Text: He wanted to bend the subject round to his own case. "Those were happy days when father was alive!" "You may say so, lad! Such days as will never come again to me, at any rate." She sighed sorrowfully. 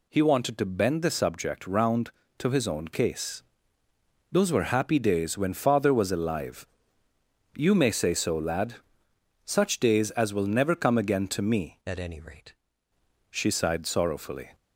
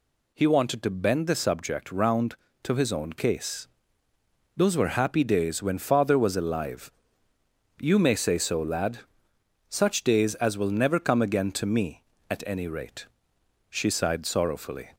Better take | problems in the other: second | changes voice from "at" to "rate"; from 11.8 to 12.5 s; 0.7 s long

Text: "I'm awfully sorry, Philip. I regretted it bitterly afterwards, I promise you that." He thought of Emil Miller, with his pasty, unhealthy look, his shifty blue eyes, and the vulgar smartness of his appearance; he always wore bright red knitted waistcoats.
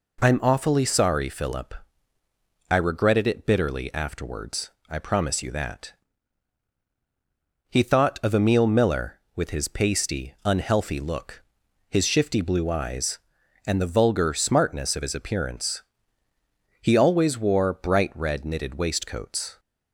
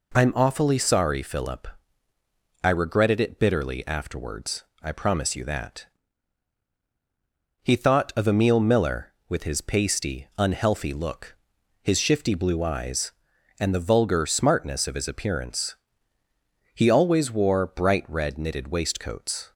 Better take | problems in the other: neither | none

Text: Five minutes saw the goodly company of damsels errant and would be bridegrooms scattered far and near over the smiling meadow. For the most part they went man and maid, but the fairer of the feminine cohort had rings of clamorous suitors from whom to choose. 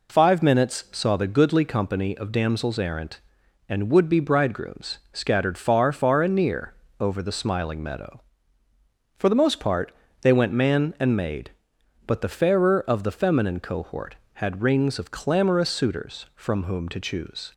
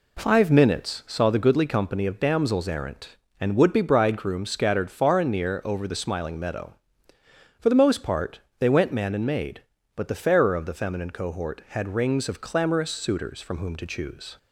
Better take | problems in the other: second | says "far" twice; at 5.9 s // pauses between "near" and "over"; slight; at 6.7 s; 0.24 s long // pauses between "part" and "they"; slight; at 9.9 s; 0.30 s long; slight in the second

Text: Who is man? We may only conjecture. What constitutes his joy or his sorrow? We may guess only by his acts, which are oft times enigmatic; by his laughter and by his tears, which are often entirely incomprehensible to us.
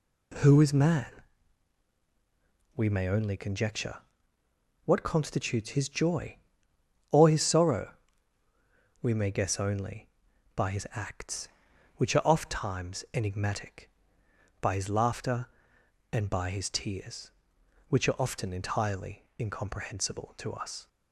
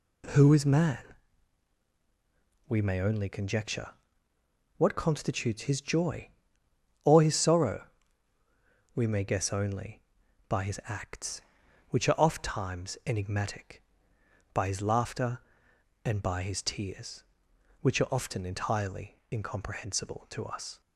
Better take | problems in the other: neither | none

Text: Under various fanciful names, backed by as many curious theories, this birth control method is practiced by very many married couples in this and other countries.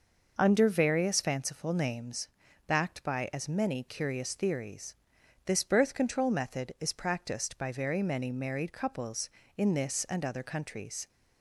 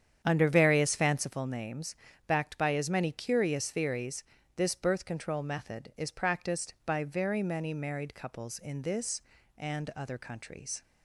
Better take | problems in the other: first | starts louder than the rest; strong; until 1.4 s; 8.5 dB

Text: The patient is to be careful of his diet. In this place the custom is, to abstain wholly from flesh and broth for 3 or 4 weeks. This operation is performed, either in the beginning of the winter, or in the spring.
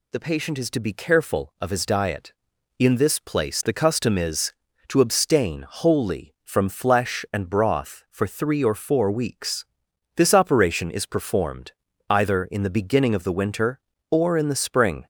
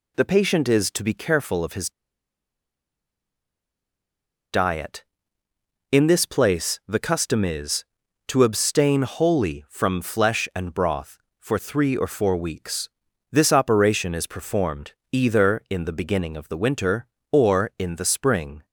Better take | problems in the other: first | pauses between "his" and "diet"; strong; at 1.8 s; 2.6 s long

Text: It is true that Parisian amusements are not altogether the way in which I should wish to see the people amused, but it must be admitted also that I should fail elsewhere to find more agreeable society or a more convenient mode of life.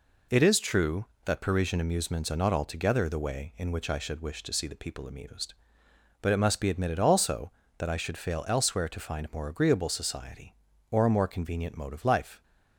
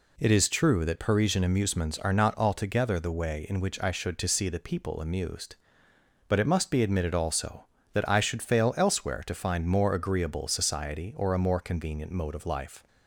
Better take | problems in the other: first | skips "wish"; at 4.1 s

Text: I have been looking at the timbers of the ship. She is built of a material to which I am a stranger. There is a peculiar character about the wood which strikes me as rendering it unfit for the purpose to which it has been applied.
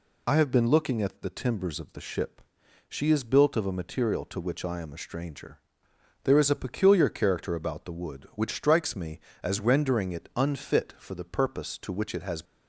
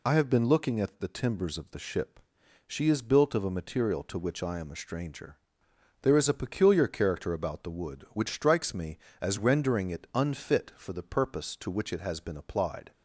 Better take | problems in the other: second | stops before "been applied"; at 12.4 s

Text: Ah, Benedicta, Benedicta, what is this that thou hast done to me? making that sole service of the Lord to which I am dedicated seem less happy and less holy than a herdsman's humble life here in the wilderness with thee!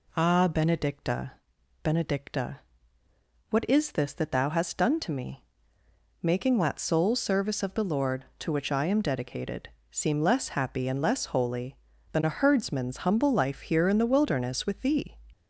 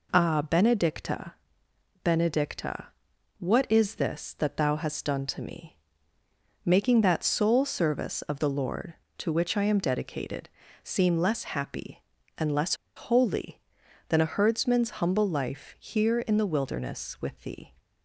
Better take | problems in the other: first | pauses between "dedicated" and "seem"; slight; at 10.4 s; 0.34 s long; slight in the first // pauses between "less" and "holy"; slight; at 12.7 s; 0.22 s long

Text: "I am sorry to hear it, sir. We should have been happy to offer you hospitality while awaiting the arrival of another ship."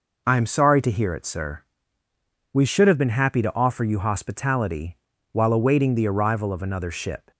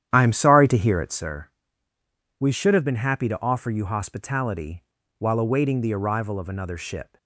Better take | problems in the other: first | starts louder than the rest; strong; until 1.3 s; 10.5 dB // pauses between "hospitality" and "while"; slight; at 4.8 s; 0.36 s long; slight in the first

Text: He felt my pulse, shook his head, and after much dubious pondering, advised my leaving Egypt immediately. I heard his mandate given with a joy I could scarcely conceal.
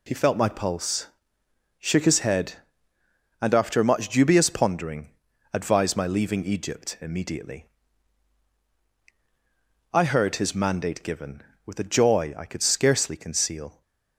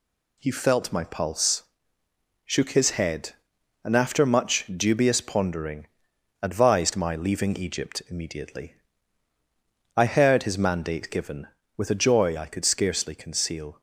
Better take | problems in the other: neither | none

